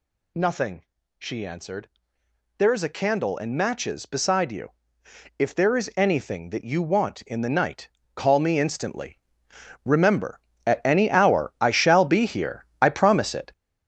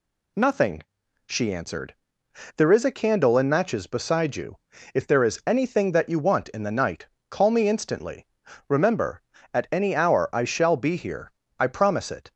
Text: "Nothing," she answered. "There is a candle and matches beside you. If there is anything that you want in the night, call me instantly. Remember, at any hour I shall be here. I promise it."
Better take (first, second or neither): second